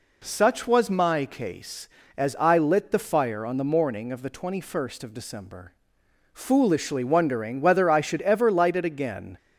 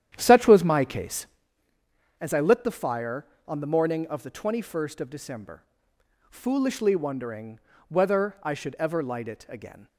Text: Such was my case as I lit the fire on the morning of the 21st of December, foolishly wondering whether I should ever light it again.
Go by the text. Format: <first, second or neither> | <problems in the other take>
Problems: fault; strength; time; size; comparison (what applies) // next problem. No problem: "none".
first | starts louder than the rest; strong; until 1.5 s; 10 dB // pauses between "wondering" and "whether"; slight; at 7.5 s; 0.30 s long